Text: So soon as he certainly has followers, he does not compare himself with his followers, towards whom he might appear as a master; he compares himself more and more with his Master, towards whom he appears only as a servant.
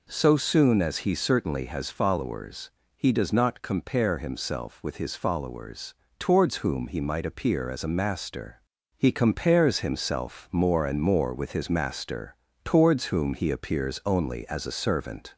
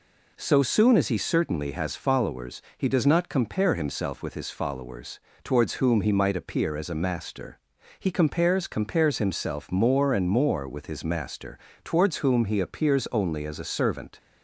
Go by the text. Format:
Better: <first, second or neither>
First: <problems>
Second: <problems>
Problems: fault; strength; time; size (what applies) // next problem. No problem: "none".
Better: first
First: none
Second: says "compares" twice; at 8.6 s